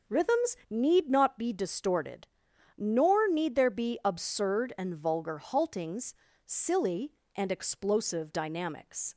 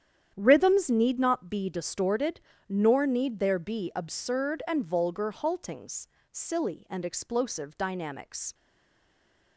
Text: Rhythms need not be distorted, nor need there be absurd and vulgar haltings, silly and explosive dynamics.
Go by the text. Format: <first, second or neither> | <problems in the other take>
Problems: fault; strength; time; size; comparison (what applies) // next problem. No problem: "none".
first | starts louder than the rest; strong; until 1.3 s; 9.5 dB // stays silent after the last word; from 8.5 s on; 1.0 s long